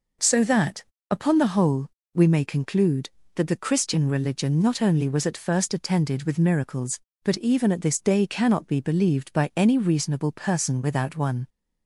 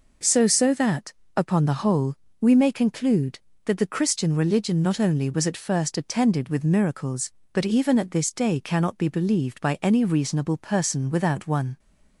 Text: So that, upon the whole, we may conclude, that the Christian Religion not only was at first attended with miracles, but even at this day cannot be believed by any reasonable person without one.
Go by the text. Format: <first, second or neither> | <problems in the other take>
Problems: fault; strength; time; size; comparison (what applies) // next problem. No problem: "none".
first | says "So" twice; at 0.4 s